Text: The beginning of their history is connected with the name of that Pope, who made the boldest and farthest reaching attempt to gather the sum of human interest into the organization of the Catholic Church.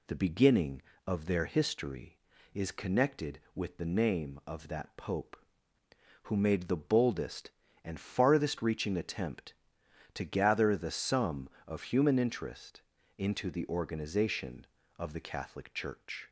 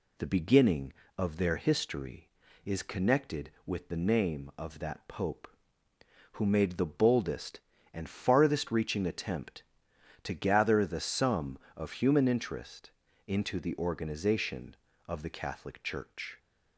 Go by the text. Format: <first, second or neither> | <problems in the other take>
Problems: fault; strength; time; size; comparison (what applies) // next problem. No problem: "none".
neither | pauses between "interest" and "into"; slight; the same in both